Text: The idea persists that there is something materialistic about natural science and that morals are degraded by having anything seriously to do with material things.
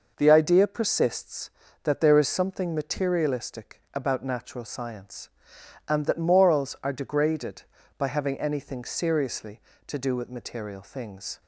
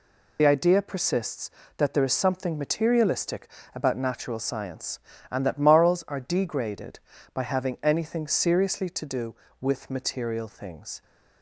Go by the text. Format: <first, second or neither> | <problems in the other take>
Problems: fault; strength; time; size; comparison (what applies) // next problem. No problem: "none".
first | loses the start of "The"; at 0.3 s; 45 ms // pauses between "materialistic" and "about"; slight; at 3.4 s; 0.26 s long